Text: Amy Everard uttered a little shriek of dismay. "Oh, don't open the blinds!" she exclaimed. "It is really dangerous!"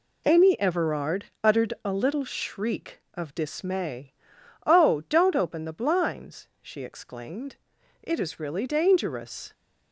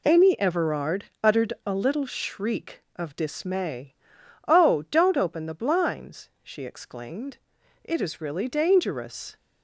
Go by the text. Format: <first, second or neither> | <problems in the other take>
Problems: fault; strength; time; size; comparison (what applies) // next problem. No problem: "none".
neither | pauses between "Everard" and "uttered"; slight; the same in both